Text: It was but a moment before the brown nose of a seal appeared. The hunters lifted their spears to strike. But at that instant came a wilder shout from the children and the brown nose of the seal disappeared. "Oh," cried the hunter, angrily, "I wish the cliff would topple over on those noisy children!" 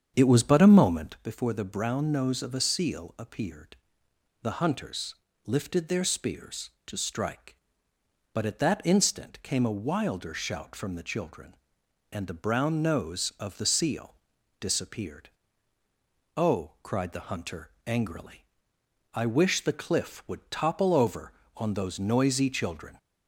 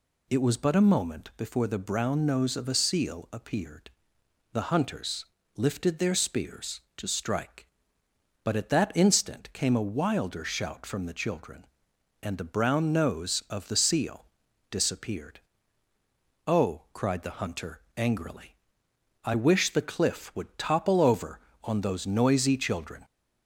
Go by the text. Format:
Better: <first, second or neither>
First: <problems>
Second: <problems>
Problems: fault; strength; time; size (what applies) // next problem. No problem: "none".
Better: second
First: starts louder than the rest; strong; until 1.2 s; 7.5 dB // pauses between "hunters" and "lifted"; slight; at 5.1 s; 0.32 s long // pauses between "seal" and "disappeared"; at 14.1 s; 0.44 s long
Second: pauses between "hunters" and "lifted"; slight; at 5.2 s; 0.32 s long // pauses between "seal" and "disappeared"; at 14.2 s; 0.44 s long